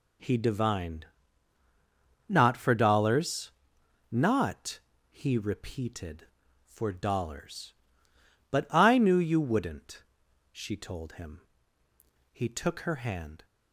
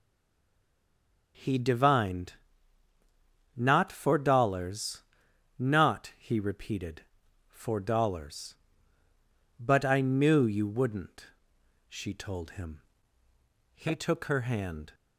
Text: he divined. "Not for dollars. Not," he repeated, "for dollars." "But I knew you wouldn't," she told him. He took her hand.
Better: first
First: none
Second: stays silent before the first word; noticeable; until 1.3 s; 1.3 s long

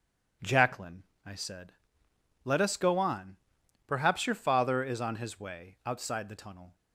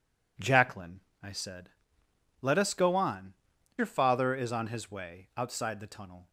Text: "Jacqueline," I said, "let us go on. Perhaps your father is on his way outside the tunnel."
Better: first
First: none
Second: skips "Perhaps"; at 3.5 s

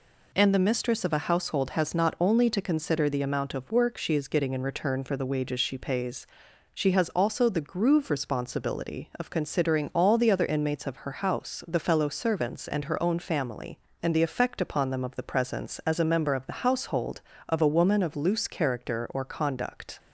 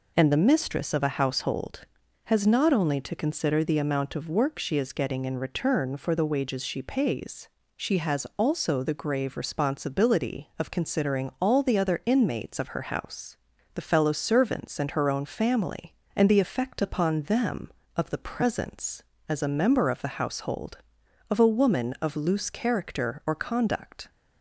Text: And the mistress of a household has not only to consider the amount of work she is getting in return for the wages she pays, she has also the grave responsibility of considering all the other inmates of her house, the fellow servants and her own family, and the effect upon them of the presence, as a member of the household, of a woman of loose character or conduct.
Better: second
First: says "groove" for "grave"; at 7.6 s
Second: none

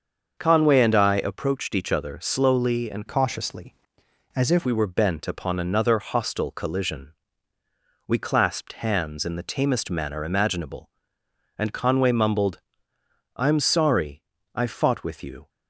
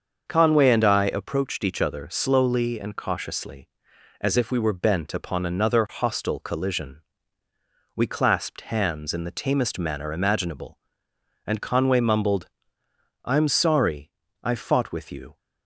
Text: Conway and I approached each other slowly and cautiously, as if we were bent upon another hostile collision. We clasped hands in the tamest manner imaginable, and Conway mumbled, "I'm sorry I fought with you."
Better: second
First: starts louder than the rest; until 1.3 s; 6.5 dB // changes voice from "cautiously" to "if"; from 3.0 to 4.6 s; 1.6 s long // pauses between "sorry" and "I"; slight; at 14.2 s; 0.32 s long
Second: starts louder than the rest; until 1.2 s; 6.5 dB // pauses between "sorry" and "I"; slight; at 14.1 s; 0.32 s long

